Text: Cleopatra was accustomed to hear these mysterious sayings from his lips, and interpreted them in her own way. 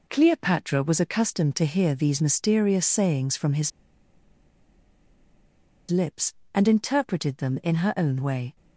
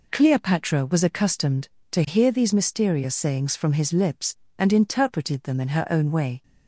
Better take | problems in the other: second | pauses between "his" and "lips"; strong; at 3.7 s; 2.2 s long

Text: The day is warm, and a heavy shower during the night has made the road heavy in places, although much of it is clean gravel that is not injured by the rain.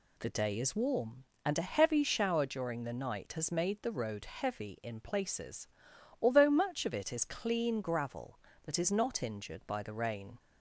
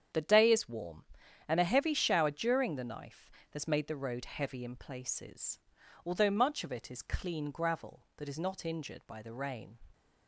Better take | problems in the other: first | starts louder than the rest; strong; until 1.5 s; 8.5 dB // says "knife" for "night"; at 2.8 s

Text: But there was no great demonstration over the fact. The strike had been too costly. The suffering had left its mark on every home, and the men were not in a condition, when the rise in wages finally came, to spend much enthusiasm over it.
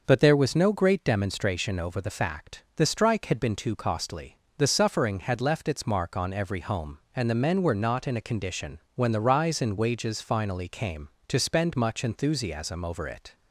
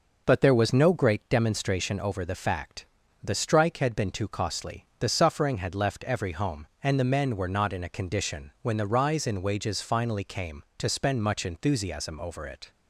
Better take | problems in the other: first | skips "its mark on"; at 6.0 s

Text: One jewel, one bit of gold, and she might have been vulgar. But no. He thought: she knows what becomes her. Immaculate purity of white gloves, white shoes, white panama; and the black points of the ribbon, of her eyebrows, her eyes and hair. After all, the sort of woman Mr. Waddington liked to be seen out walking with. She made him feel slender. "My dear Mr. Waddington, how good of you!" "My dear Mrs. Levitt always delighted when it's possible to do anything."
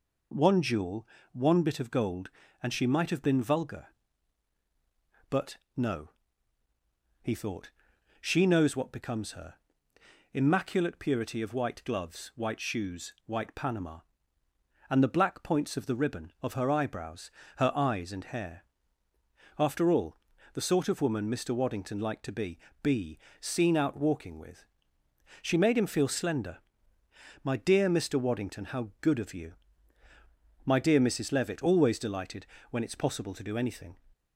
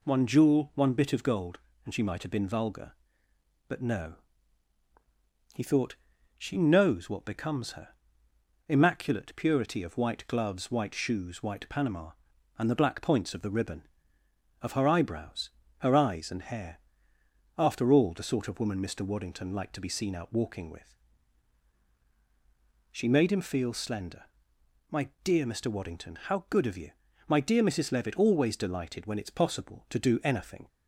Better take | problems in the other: second | pauses between "But" and "no"; slight; at 5.5 s; 0.18 s long // says "be" twice; at 22.8 s // pauses between "delighted" and "when"; slight; at 32.4 s; 0.24 s long

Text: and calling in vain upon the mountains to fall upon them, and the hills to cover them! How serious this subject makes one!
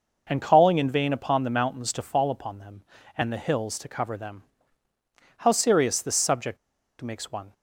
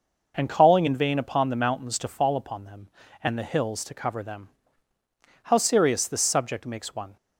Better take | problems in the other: second | pauses between "subject" and "makes"; at 6.5 s; 0.43 s long

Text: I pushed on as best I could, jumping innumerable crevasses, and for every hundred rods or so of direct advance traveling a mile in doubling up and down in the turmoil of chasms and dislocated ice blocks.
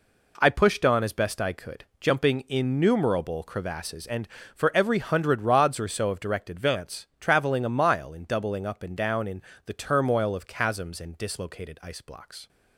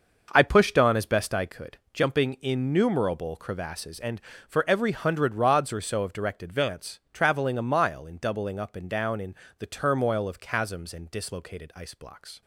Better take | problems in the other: first | starts louder than the rest; until 1.6 s; 6 dB // pauses between "in" and "the"; slight; at 9.3 s; 0.24 s long; slight in the first

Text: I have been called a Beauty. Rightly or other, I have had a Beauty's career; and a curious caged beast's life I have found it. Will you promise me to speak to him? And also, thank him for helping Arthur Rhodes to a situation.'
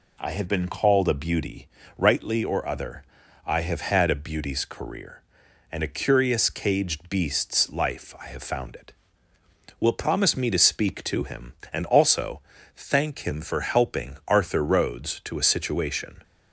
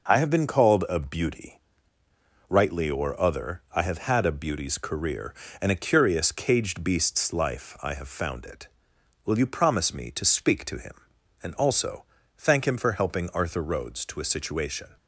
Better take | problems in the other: second | skips "you"; at 9.9 s

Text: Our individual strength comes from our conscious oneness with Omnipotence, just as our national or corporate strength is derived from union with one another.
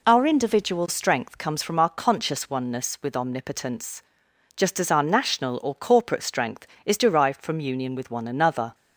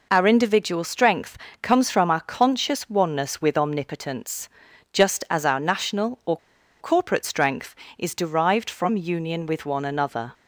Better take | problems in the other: first | pauses between "strength" and "comes"; slight; at 1.3 s; 0.24 s long // pauses between "or" and "corporate"; at 6.3 s; 0.43 s long

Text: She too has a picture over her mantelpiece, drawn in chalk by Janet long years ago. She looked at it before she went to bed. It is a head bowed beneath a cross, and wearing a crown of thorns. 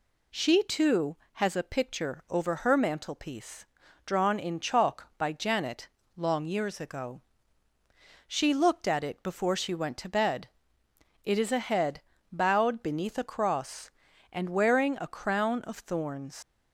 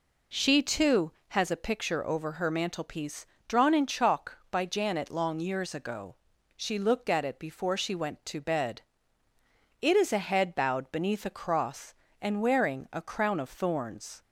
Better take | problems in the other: second | pauses between "Janet" and "long"; slight; at 5.8 s; 0.30 s long // pauses between "head" and "bowed"; slight; at 12.0 s; 0.30 s long // leaves "thorns" unfinished; at 16.4 s; 75 ms

